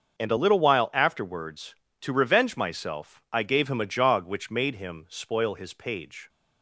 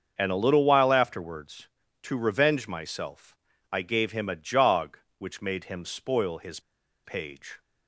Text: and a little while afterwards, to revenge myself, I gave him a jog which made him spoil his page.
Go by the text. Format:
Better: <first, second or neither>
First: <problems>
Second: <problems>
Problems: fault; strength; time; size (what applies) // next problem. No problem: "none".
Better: first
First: starts louder than the rest; until 1.2 s; 6.5 dB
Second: starts louder than the rest; until 1.1 s; 6.5 dB // pauses between "his" and "page"; at 6.5 s; 0.45 s long